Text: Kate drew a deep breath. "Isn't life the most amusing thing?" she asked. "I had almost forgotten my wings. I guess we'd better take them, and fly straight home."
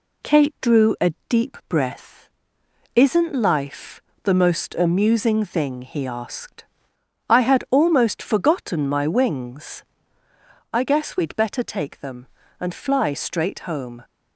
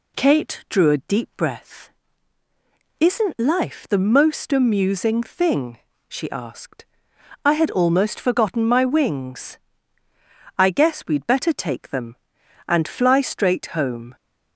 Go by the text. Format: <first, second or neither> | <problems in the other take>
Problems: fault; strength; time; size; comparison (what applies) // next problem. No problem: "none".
second | pauses between "a" and "deep"; slight; at 1.1 s; 0.16 s long // pauses between "life" and "the"; slight; at 4.0 s; 0.18 s long // says "he" for "she"; at 5.8 s